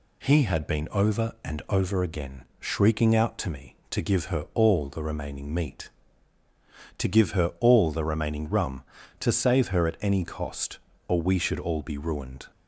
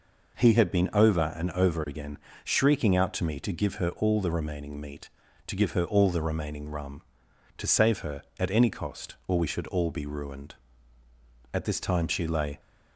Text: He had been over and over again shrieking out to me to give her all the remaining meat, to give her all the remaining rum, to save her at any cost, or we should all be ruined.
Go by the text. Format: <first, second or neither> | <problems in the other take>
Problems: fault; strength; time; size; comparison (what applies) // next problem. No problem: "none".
first | pauses between "again" and "shrieking"; slight; at 2.1 s; 0.26 s long; slight in the first // goes on to say "At this time she lay"; noticeable; from 11.5 s on; 1.0 s long